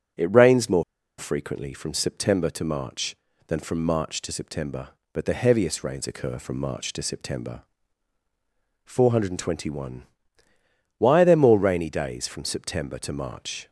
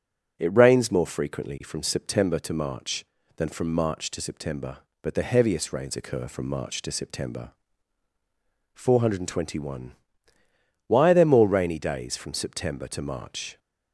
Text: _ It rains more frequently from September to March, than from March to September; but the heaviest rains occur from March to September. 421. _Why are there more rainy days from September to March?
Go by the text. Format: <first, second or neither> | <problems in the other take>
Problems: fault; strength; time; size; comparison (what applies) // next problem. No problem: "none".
second | starts louder than the rest; noticeable; until 1.5 s; 6 dB // pauses between "more" and "frequently"; slight; at 0.8 s; 0.35 s long